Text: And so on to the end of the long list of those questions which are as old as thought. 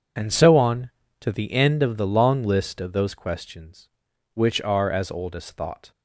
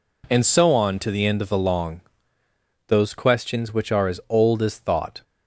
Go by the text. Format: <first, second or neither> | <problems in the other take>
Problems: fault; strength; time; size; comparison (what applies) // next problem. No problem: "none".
first | skips "list of"; at 2.4 s